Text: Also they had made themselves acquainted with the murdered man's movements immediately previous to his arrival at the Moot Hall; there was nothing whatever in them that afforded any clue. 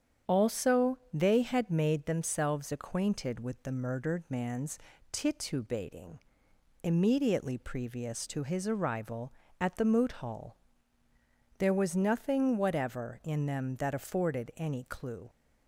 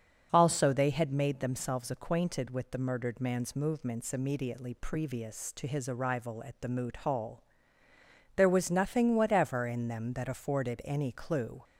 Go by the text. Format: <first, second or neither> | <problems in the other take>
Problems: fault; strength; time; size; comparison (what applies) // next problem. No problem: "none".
second | starts louder than the rest; strong; until 1.4 s; 8 dB; also in the second // says "titubating" for "movements"; at 5.1 s